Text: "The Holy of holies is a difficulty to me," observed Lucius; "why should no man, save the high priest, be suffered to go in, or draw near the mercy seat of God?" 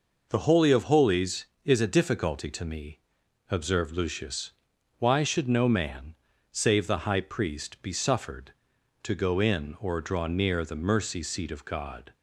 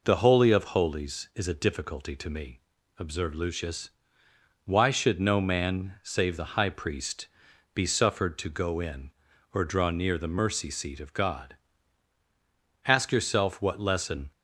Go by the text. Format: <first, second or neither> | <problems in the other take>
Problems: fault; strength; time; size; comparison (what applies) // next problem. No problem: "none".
first | goes on to say "Ask yourself what lesson"; from 12.8 s on; 1.4 s long